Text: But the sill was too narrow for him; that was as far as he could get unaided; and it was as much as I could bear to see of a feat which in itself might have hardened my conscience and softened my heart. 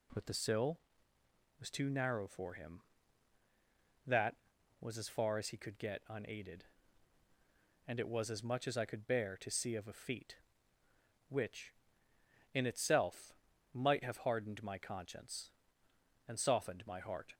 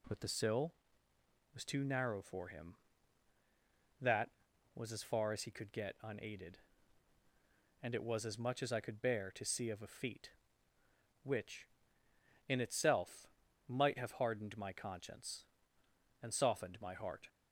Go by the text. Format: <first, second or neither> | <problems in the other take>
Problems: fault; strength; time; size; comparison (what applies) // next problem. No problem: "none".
neither | pauses between "itself" and "might"; the same in both